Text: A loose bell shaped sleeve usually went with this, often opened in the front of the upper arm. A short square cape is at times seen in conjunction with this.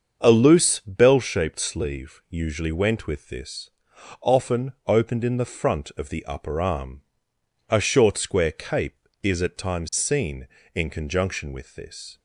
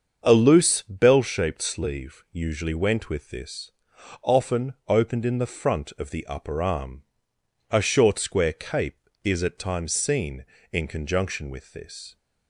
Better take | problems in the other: neither | starts louder than the rest; the same in both // pauses between "often" and "opened"; slight; the same in both

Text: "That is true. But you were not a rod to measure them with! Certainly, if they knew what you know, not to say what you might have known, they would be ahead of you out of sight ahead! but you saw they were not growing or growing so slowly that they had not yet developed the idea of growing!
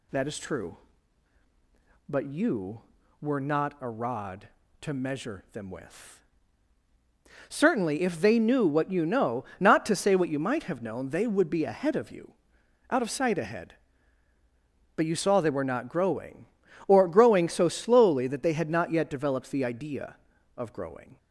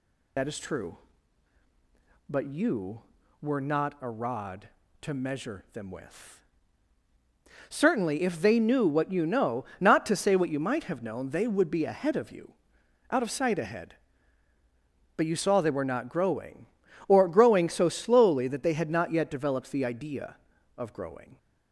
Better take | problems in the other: first | loses the start of "That"; at 0.3 s; 55 ms // pauses between "you" and "out"; noticeable; at 12.5 s; 0.56 s long; noticeable in the first

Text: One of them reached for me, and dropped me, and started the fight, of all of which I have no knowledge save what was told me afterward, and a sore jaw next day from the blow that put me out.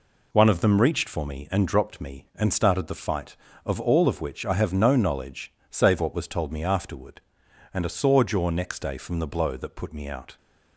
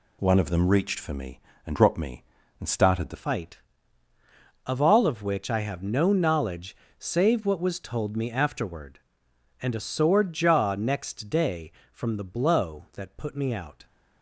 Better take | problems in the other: first | changes voice at "fight"; from 3.1 s on; 10.7 s long // pauses between "knowledge" and "save"; slight; at 6.7 s; 0.24 s long; slight in the first

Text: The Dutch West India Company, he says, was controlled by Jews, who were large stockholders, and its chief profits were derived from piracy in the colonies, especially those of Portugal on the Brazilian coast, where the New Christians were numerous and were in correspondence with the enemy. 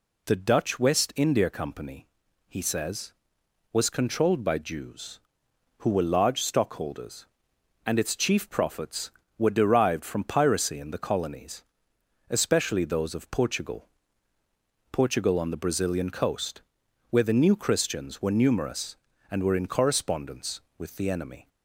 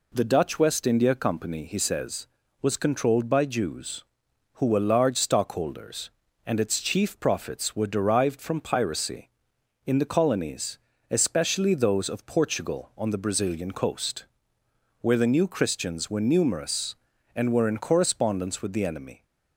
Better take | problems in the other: second | says "Portugal" twice; at 14.9 s

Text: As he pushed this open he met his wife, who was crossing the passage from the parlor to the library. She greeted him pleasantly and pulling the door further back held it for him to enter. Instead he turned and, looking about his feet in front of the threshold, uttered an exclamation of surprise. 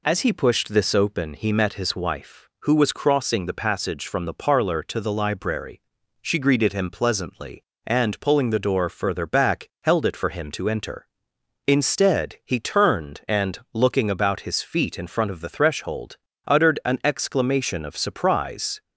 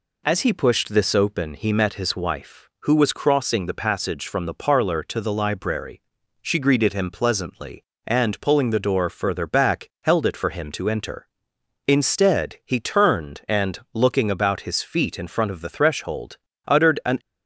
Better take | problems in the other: first | stops before "exclamation of surprise"; at 17.1 s

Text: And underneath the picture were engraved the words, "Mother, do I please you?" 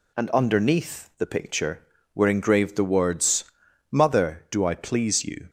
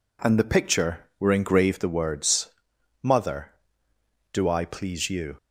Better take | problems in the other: first | skips "underneath"; at 0.3 s

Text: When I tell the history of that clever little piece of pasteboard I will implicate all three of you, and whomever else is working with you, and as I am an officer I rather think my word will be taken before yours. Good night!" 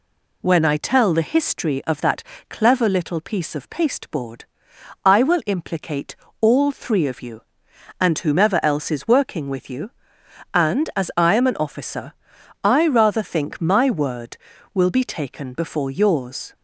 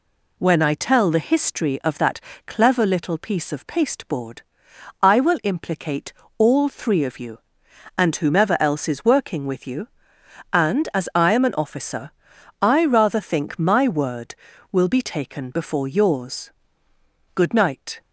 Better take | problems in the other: second | pauses between "that" and "clever"; slight; at 2.2 s; 0.28 s long; slight in the second // pauses between "pasteboard" and "I"; noticeable; at 4.4 s; 0.60 s long; noticeable in the second // pauses between "implicate" and "all"; slight; at 6.1 s; 0.26 s long; slight in the second // pauses between "officer" and "I"; noticeable; at 12.1 s; 0.50 s long; noticeable in the second // stops before "Good night"; at 16.5 s

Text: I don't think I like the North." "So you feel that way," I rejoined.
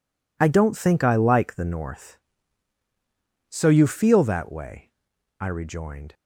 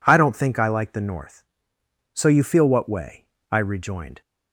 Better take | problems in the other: first | says "what" for "that"; at 2.6 s

